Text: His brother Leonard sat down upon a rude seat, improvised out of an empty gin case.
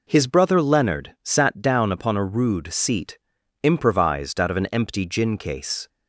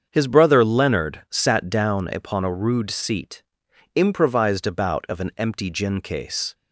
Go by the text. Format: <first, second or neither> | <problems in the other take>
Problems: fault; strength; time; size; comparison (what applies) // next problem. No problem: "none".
first | starts louder than the rest; until 1.1 s; 7 dB // says "about" for "out"; at 4.6 s